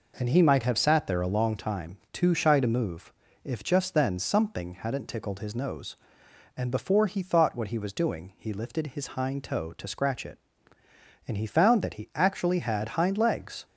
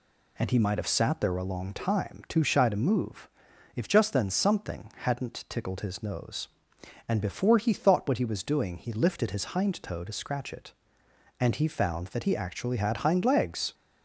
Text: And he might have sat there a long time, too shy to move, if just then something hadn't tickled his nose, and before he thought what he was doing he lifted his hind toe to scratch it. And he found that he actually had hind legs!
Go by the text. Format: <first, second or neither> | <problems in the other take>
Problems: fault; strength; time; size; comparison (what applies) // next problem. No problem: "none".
neither | none